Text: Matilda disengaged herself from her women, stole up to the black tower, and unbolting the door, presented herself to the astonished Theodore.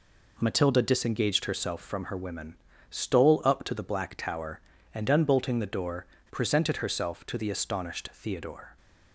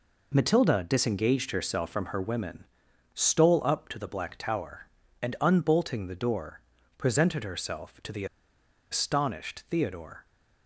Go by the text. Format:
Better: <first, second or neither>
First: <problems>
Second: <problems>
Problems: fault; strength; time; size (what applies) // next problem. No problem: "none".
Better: first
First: none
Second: pauses between "the" and "astonished"; noticeable; at 8.2 s; 0.66 s long